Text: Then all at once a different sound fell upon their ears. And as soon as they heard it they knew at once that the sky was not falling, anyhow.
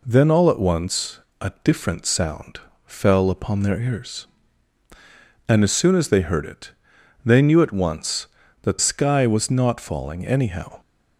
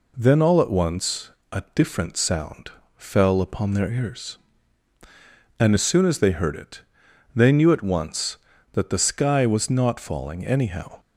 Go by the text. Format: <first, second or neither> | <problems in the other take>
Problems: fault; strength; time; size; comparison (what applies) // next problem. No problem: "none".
second | pauses between "once" and "a"; slight; at 1.1 s; 0.20 s long; slight in the second // pauses between "sound" and "fell"; slight; at 2.5 s; 0.26 s long; slight in the second // pauses between "it" and "they"; noticeable; at 6.7 s; 0.52 s long; noticeable in the second // skips "the"; at 8.7 s